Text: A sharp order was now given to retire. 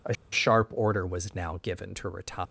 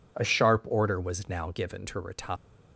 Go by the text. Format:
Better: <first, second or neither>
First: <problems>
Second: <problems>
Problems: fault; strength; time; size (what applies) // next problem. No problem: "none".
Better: second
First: pauses between "A" and "sharp"; slight; at 0.1 s; 0.19 s long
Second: none